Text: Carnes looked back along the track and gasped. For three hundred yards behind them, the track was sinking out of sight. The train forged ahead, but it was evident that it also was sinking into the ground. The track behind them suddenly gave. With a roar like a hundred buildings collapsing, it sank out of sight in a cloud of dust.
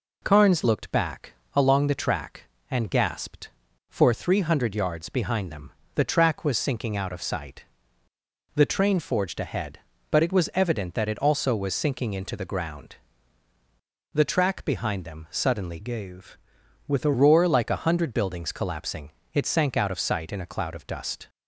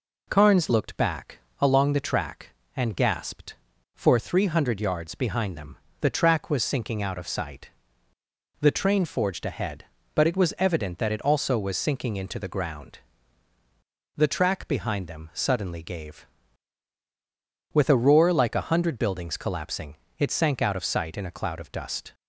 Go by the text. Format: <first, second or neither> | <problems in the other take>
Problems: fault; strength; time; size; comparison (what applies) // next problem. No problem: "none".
second | pauses between "back" and "along"; slight; at 1.3 s; 0.20 s long; slight in the second // changes voice from "gave" to "a"; from 15.8 to 17.1 s; 1.3 s long